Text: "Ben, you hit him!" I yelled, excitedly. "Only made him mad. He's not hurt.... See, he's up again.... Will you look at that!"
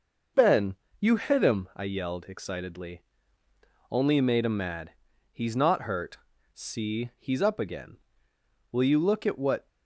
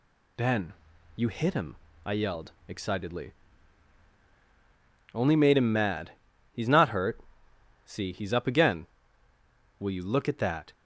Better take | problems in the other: second | says "what" for "that"; at 9.3 s

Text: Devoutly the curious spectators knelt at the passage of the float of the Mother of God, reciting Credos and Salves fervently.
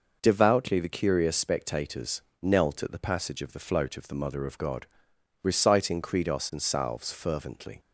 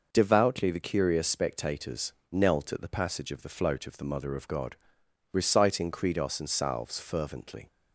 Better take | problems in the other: neither | pauses between "spectators" and "knelt"; slight; the same in both

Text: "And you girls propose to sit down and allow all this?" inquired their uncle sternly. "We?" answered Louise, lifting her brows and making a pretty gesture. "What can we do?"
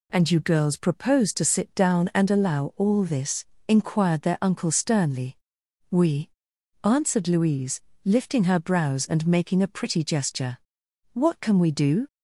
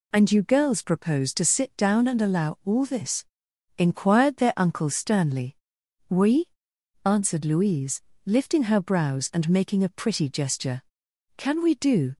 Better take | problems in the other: first | skips "What"; at 11.0 s

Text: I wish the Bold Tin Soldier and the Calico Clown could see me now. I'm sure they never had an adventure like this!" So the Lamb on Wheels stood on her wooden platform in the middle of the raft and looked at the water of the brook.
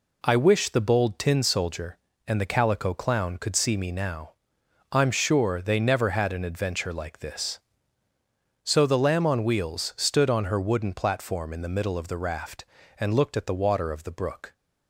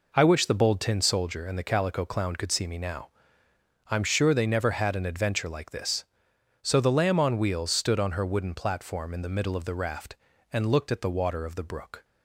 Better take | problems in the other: neither | none

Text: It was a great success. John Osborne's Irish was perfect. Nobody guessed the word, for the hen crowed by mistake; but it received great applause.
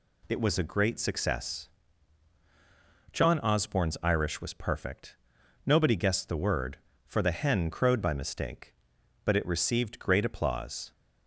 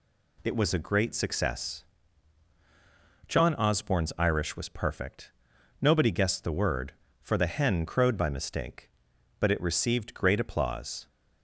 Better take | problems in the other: neither | none

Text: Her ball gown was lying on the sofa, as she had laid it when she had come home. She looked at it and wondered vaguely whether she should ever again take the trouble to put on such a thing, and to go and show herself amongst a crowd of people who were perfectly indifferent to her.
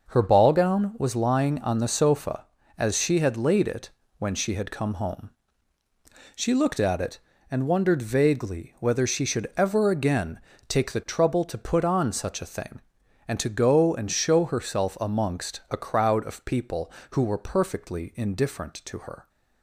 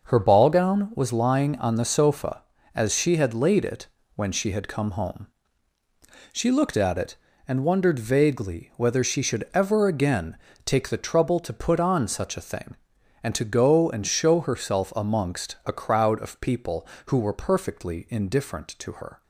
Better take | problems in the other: neither | pauses between "it" and "when"; slight; the same in both // pauses between "again" and "take"; slight; the same in both

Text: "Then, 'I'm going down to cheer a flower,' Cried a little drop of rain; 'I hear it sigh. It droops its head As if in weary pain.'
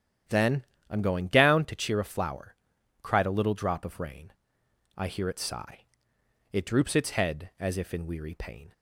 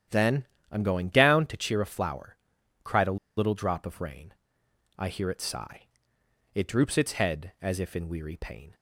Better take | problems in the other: first | starts louder than the rest; strong; until 1.3 s; 10 dB; strong in the first // pauses between "a" and "little"; slight; at 3.1 s; 0.19 s long

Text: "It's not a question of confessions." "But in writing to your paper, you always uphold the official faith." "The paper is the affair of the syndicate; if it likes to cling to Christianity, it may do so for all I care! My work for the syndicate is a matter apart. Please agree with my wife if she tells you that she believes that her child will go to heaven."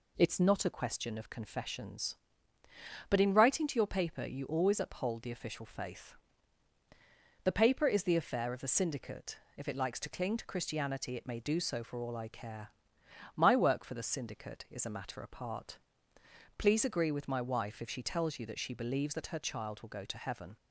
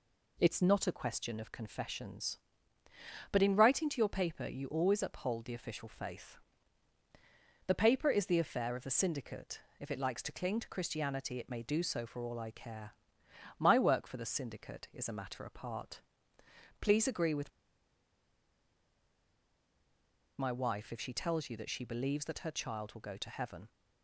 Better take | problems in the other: first | pauses between "with" and "my"; strong; at 17.5 s; 2.8 s long

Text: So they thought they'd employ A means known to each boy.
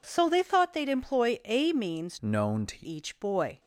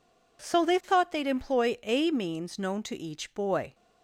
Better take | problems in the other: second | changes voice from "known" to "to"; from 2.2 to 2.7 s; 0.5 s long

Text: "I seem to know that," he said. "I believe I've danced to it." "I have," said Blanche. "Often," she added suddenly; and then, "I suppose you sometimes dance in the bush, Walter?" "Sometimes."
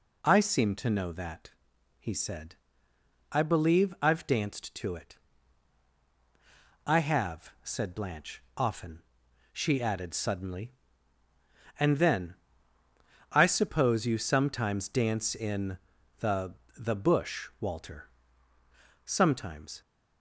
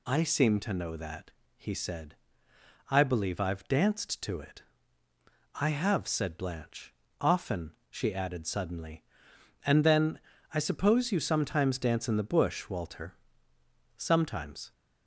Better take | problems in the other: second | pauses between "in" and "the"; at 15.7 s; 0.40 s long // says "the" twice; at 16.7 s

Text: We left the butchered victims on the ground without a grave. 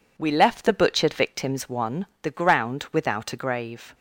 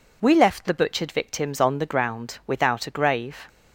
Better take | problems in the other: second | says "one" for "on"; at 1.6 s

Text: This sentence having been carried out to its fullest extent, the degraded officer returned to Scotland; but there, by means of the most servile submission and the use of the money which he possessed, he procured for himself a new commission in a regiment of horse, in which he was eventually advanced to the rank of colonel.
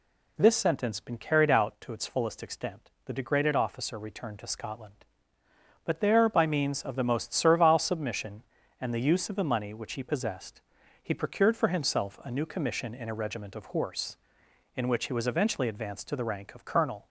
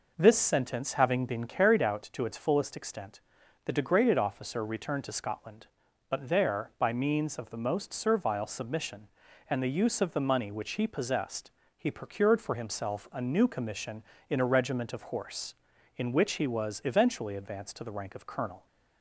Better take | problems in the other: second | skips "having"; at 0.9 s

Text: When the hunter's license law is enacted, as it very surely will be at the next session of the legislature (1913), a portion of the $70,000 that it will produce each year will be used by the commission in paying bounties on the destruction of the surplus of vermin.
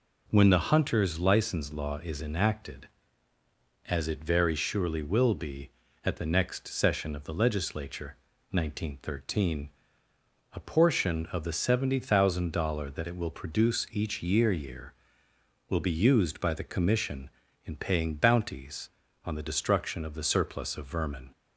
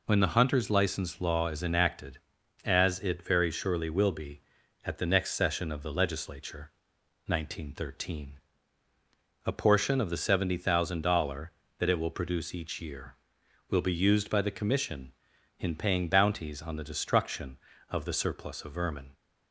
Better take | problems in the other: second | says "year" twice; at 14.5 s

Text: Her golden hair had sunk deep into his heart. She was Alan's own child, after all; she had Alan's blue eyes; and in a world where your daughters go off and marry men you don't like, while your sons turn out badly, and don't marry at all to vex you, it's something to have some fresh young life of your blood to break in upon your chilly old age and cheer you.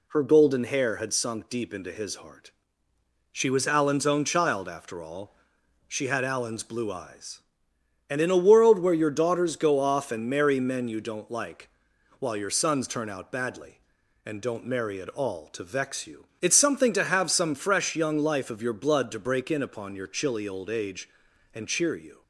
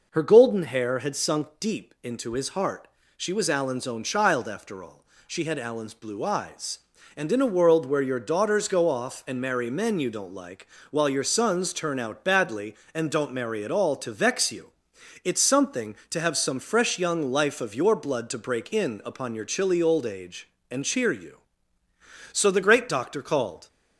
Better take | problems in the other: first | goes on to say "So the great doctor called"; from 22.3 s on; 1.3 s long

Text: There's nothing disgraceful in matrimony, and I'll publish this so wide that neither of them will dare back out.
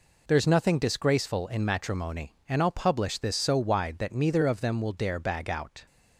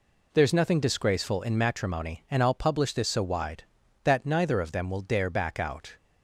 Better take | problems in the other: second | says "bag" for "back"; at 5.1 s

